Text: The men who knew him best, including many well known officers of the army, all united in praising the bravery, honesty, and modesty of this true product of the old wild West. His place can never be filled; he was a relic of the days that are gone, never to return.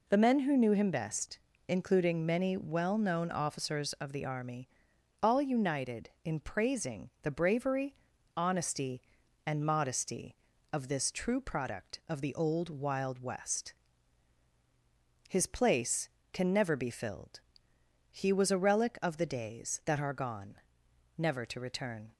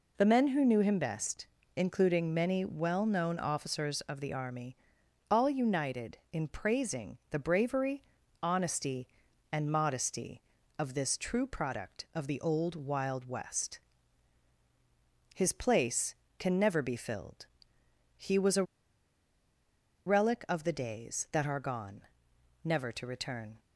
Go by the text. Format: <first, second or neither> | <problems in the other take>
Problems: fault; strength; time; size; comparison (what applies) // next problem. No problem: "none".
first | pauses between "a" and "relic"; strong; at 18.6 s; 1.4 s long